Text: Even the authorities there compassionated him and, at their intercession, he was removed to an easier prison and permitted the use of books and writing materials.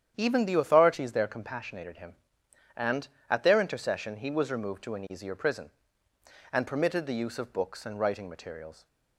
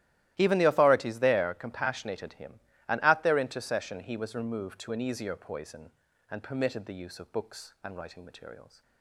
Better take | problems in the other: first | starts louder than the rest; strong; until 1.3 s; 14.5 dB; strong in the first // says "poison" for "prison"; at 5.3 s

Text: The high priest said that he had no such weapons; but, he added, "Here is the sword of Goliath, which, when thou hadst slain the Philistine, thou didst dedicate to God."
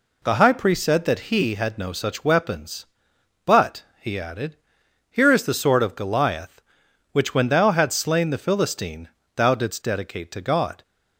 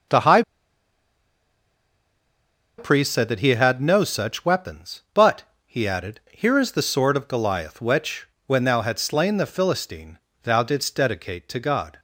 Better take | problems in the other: first | pauses between "high" and "priest"; strong; at 0.4 s; 2.3 s long

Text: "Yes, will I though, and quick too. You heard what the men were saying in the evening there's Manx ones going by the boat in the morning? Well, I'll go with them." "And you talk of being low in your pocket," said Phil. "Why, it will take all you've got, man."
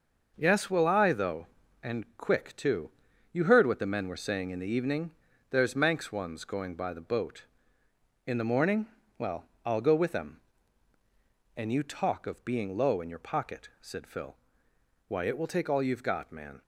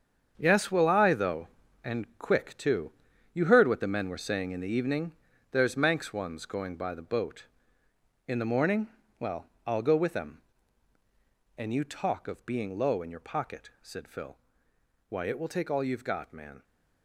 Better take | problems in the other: first | gets quieter; strong; throughout; 11 dB // pauses between "evening" and "there's"; at 5.1 s; 0.38 s long; also in the first

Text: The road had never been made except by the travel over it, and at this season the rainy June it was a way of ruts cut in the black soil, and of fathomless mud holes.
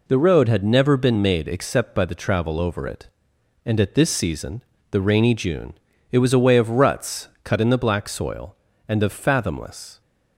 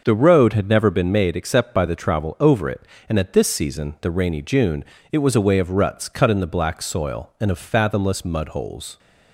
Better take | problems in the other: second | pauses between "season" and "the"; slight; at 4.6 s; 0.30 s long // pauses between "June" and "it"; at 5.7 s; 0.38 s long; slight in the second // pauses between "ruts" and "cut"; slight; at 7.2 s; 0.15 s long // stops before "mud holes"; at 10.0 s

